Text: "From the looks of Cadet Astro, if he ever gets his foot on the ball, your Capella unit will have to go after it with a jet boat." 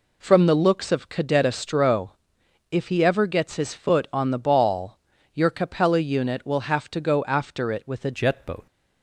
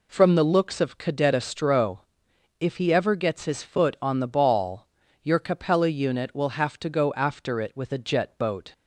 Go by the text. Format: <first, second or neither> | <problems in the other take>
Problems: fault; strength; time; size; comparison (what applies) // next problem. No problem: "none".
second | changes voice at "jet"; from 8.1 s on; 0.5 s long